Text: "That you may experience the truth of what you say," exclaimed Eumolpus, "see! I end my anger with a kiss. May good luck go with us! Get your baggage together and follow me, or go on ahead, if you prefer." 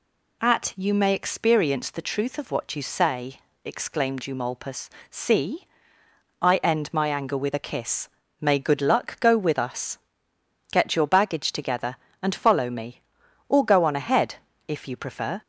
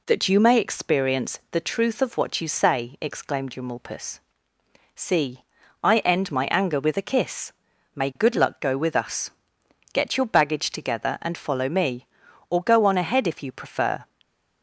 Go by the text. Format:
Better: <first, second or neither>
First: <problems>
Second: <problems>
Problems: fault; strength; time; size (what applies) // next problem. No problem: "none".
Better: second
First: says "At" for "That"; at 0.4 s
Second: none